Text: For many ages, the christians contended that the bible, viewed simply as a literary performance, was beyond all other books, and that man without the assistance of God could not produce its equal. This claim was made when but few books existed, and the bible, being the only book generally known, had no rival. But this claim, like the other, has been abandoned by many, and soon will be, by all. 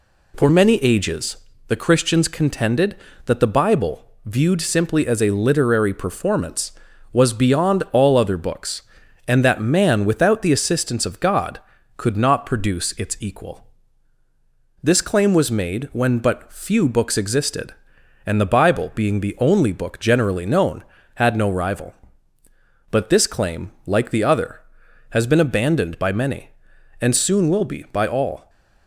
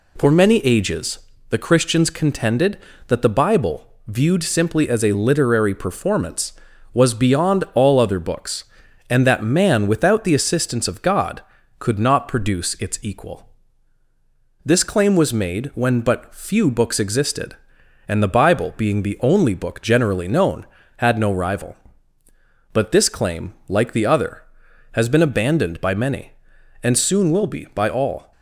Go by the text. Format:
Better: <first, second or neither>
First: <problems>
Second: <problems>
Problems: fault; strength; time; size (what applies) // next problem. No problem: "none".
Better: neither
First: none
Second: none